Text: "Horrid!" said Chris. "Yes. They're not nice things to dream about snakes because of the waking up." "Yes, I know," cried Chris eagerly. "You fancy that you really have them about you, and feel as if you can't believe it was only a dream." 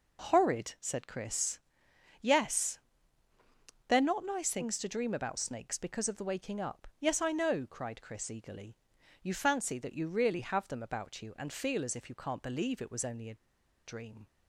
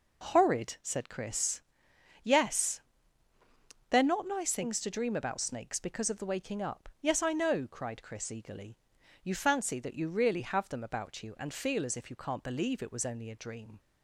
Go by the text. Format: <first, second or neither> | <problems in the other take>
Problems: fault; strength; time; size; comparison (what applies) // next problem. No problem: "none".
second | pauses between "a" and "dream"; noticeable; at 13.3 s; 0.50 s long